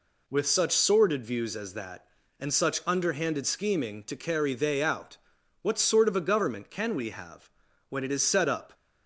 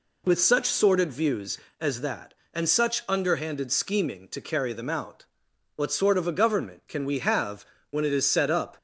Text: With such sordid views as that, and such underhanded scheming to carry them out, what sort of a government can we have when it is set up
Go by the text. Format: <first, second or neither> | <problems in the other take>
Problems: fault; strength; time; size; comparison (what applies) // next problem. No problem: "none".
second | says "they" for "them"; at 4.5 s // pauses between "have" and "when"; at 7.4 s; 0.42 s long; slight in the second